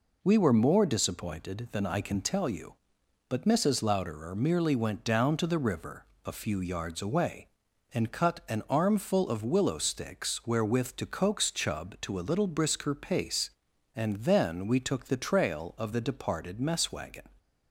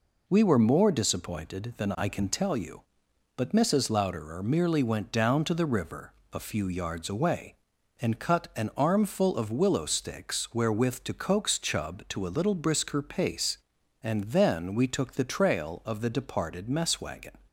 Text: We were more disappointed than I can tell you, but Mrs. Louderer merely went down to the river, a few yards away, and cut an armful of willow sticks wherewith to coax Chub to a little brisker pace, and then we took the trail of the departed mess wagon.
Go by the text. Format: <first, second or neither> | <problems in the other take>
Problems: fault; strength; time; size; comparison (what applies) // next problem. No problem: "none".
neither | none